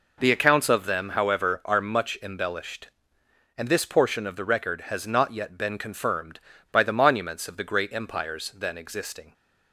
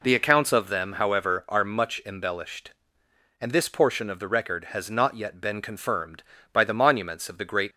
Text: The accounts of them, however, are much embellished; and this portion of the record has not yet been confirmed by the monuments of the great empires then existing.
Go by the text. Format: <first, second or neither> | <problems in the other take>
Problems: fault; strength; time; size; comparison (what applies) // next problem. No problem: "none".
first | stops before "empires then existing"; at 7.7 s